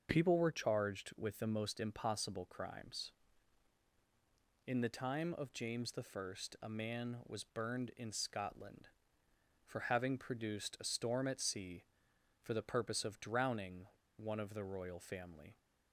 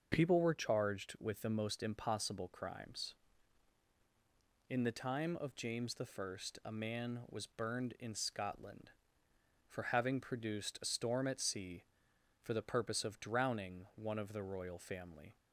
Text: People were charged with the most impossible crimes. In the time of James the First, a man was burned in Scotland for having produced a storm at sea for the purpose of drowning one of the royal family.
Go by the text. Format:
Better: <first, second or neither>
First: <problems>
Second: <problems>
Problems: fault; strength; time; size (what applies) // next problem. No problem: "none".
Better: second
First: starts louder than the rest; until 1.1 s; 6.5 dB // pauses between "drowning" and "one"; slight; at 13.8 s; 0.33 s long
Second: starts louder than the rest; until 1.1 s; 6.5 dB